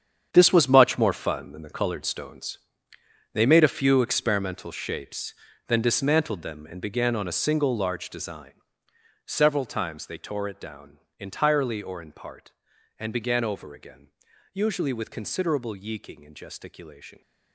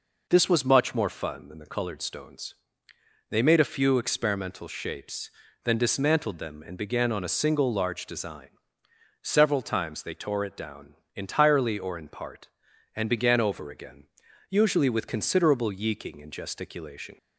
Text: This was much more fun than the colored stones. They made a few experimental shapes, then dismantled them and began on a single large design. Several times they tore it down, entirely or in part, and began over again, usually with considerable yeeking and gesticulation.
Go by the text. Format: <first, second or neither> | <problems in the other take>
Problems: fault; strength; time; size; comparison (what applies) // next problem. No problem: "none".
second | gets quieter; strong; throughout; 12 dB